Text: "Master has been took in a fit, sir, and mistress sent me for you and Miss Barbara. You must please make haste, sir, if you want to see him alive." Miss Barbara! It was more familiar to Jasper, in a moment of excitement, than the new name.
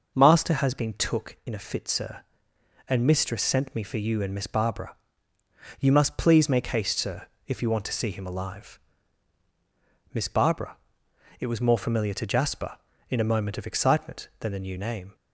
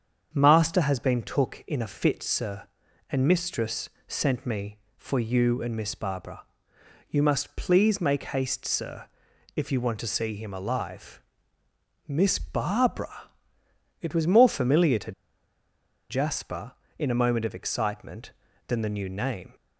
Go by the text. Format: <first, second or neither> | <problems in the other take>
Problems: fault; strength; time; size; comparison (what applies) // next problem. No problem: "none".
first | starts louder than the rest; strong; until 1.3 s; 7.5 dB // pauses between "mistress" and "sent"; slight; at 3.9 s; 0.18 s long // pauses between "to" and "Jasper"; noticeable; at 15.1 s; 0.97 s long